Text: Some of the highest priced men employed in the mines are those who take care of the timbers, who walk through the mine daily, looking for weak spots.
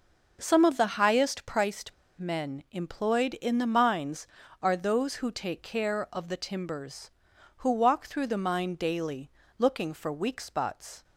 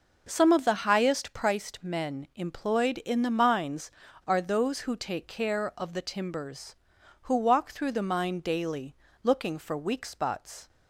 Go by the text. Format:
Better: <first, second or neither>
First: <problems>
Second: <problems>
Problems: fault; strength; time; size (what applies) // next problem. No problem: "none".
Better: second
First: pauses between "priced" and "men"; slight; at 1.9 s; 0.23 s long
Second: none